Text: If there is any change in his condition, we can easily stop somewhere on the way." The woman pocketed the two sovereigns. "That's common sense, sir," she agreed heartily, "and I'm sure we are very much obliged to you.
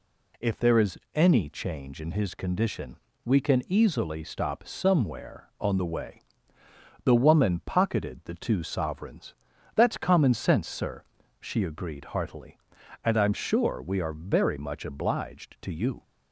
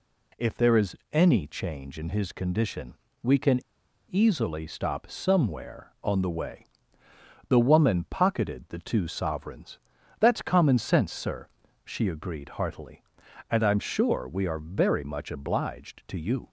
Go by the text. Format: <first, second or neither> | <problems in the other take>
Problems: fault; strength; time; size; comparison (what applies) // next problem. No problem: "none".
first | pauses between "is" and "any"; slight; at 0.9 s; 0.16 s long; slight in the first // pauses between "can" and "easily"; noticeable; at 3.6 s; 0.49 s long